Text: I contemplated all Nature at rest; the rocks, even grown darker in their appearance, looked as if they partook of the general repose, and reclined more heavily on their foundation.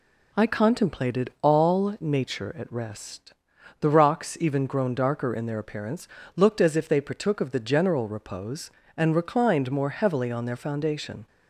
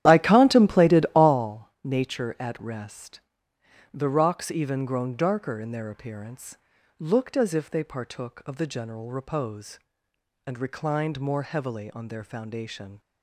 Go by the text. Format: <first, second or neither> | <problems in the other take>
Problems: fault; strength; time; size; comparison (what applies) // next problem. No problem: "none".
first | starts louder than the rest; strong; until 1.4 s; 11.5 dB